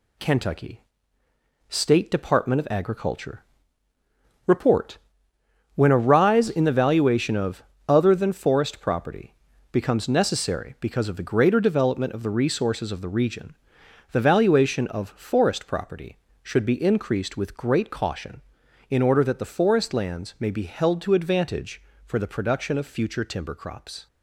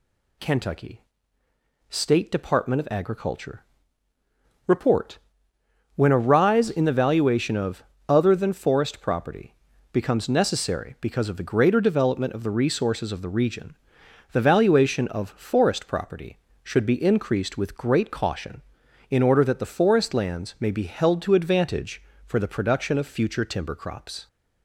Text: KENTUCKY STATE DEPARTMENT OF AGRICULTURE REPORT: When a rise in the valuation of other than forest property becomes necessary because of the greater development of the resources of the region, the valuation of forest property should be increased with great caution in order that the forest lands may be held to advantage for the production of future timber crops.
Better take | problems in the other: second | gets quieter; noticeable; throughout; 5 dB // pauses between "KENTUCKY" and "STATE"; noticeable; at 0.8 s; 0.88 s long; noticeable in the second // pauses between "AGRICULTURE" and "REPORT"; at 3.4 s; 1.0 s long; also in the second // pauses between "of" and "other"; slight; at 7.6 s; 0.24 s long; slight in the second // pauses between "property" and "becomes"; slight; at 9.3 s; 0.36 s long; slight in the second

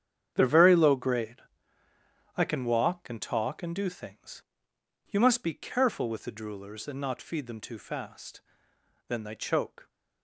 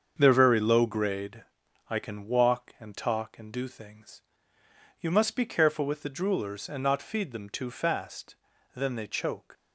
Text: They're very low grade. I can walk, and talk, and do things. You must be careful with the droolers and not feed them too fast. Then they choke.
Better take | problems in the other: second | gets quieter; strong; throughout; 12 dB // starts louder than the rest; strong; until 1.3 s; 8.5 dB; also in the second

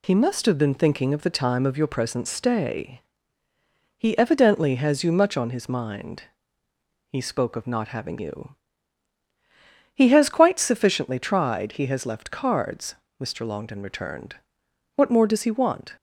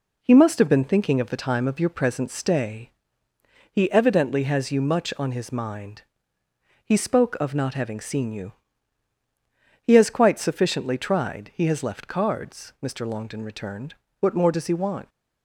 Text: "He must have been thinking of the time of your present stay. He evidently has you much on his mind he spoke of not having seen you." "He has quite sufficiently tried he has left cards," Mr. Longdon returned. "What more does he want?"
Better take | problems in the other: second | pauses between "mind" and "he"; noticeable; at 6.2 s; 0.84 s long; noticeable in the second // skips "seen"; at 8.1 s

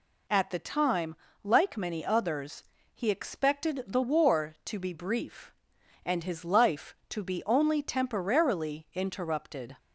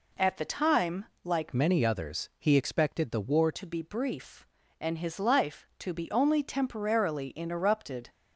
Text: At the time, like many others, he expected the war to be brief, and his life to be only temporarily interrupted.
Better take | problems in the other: first | changes voice from "many" to "war"; from 1.5 to 3.4 s; 1.9 s long

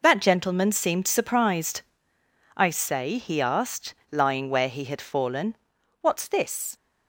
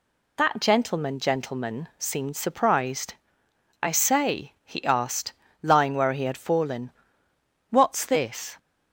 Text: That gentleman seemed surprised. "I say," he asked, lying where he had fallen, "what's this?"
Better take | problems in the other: first | says "gentleman" twice; at 1.1 s

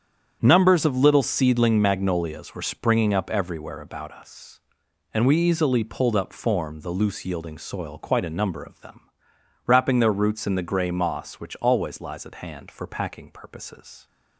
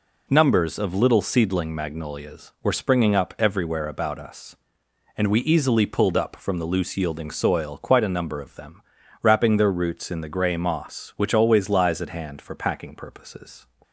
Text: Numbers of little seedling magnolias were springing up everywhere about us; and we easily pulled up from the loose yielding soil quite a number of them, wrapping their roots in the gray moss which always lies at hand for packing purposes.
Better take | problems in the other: second | starts louder than the rest; strong; until 1.4 s; 8.5 dB // says "form" for "from"; at 6.3 s

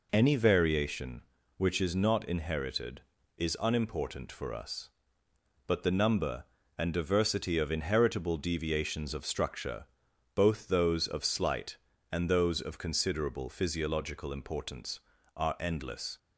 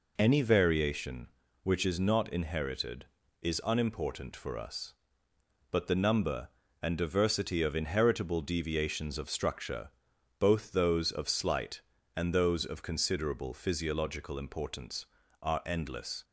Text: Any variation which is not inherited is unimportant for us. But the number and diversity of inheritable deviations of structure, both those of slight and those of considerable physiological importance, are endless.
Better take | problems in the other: neither | none

